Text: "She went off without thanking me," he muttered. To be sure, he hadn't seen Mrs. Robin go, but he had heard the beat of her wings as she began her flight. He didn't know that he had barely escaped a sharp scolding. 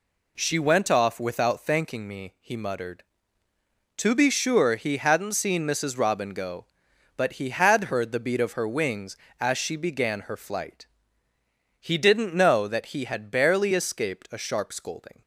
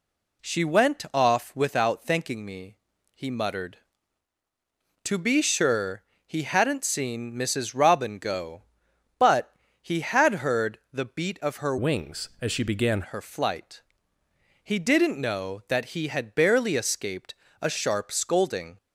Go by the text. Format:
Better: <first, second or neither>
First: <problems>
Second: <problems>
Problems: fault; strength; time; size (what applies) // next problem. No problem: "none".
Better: first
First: none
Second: pauses between "but" and "he"; slight; at 9.5 s; 0.28 s long // changes voice from "wings" to "began"; from 11.7 to 13.0 s; 1.3 s long // pauses between "escaped" and "a"; slight; at 17.3 s; 0.26 s long